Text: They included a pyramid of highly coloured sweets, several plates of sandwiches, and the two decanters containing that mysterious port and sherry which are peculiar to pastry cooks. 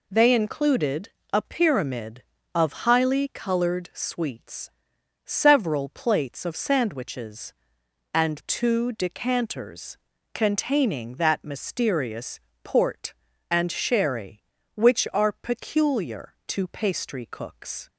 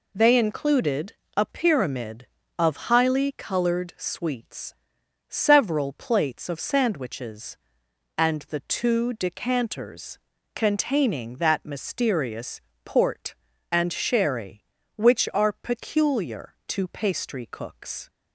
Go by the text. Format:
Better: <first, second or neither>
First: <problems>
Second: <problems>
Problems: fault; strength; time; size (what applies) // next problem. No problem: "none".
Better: second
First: pauses between "included" and "a"; slight; at 1.0 s; 0.24 s long // skips "the"; at 8.3 s // pauses between "decanters" and "containing"; at 9.9 s; 0.38 s long // pauses between "mysterious" and "port"; slight; at 12.3 s; 0.24 s long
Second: pauses between "included" and "a"; slight; at 1.1 s; 0.24 s long // pauses between "decanters" and "containing"; at 10.1 s; 0.38 s long // pauses between "mysterious" and "port"; slight; at 12.6 s; 0.24 s long